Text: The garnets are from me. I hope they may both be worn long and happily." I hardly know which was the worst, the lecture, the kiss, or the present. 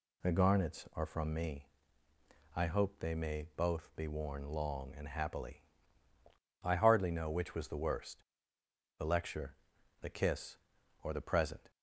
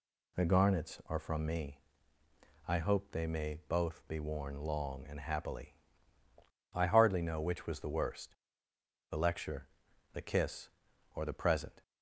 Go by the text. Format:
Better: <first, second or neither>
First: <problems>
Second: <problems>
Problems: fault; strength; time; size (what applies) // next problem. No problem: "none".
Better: neither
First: none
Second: none